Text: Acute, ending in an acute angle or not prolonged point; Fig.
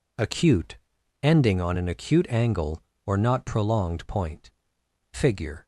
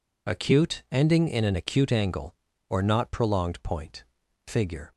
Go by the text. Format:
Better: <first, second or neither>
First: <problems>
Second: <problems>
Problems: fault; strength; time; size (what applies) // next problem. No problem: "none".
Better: second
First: says "on" for "in"; at 1.5 s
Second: none